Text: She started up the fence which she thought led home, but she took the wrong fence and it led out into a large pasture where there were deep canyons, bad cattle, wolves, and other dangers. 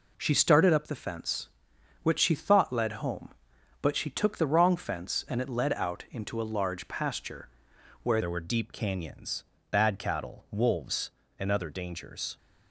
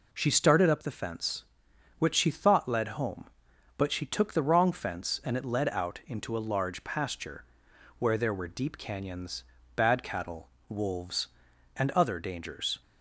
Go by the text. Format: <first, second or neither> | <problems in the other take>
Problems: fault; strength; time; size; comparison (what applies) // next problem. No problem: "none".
second | pauses between "pasture" and "where"; noticeable; at 7.4 s; 0.54 s long; noticeable in the second // changes voice at "there"; from 8.2 s on; 4.1 s long